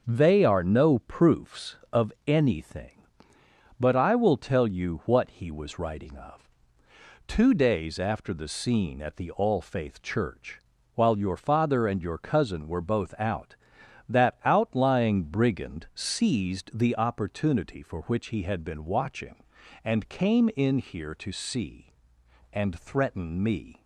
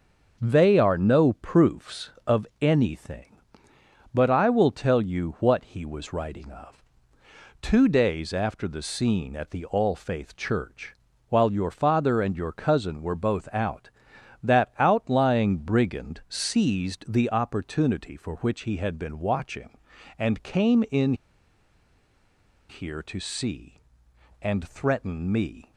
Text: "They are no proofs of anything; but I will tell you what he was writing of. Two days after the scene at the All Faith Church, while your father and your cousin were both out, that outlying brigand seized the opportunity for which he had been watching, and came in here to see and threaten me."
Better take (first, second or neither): first